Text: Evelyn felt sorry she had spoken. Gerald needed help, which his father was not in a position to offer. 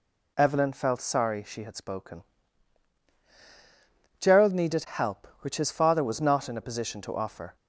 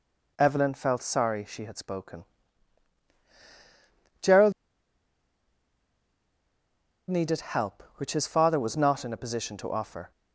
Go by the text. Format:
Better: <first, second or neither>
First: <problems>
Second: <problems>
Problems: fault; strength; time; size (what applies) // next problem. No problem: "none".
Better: first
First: none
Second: pauses between "Gerald" and "needed"; strong; at 4.5 s; 2.5 s long